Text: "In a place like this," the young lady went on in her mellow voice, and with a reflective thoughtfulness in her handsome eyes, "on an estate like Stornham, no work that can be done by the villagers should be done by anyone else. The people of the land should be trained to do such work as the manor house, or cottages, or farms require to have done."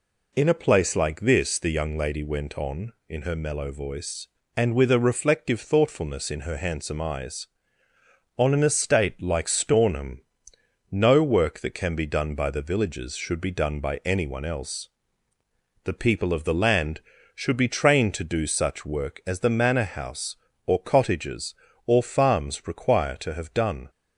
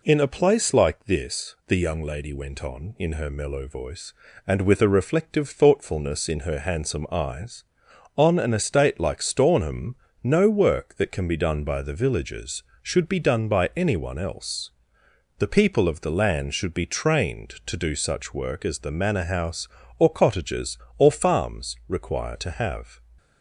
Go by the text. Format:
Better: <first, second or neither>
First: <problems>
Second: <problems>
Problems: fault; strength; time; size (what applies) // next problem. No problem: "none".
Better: first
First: none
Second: stops before "done"; at 23.1 s